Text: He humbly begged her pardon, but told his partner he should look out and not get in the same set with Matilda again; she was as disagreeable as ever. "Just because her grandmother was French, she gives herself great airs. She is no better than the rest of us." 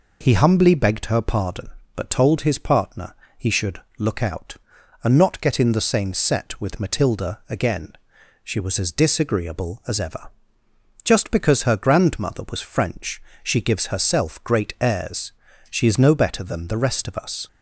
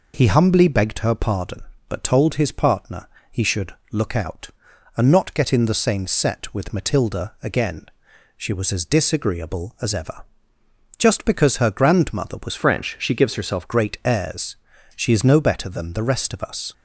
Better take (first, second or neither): first